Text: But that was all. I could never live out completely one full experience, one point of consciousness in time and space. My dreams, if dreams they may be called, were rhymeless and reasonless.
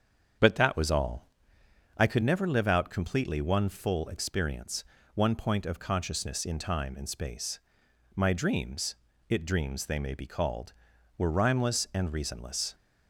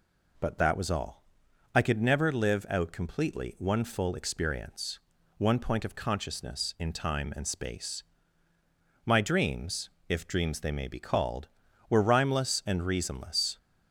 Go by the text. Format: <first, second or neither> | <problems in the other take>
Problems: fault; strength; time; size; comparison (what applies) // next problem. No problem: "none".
second | starts louder than the rest; strong; until 2.0 s; 8 dB // says "it" for "if"; at 9.2 s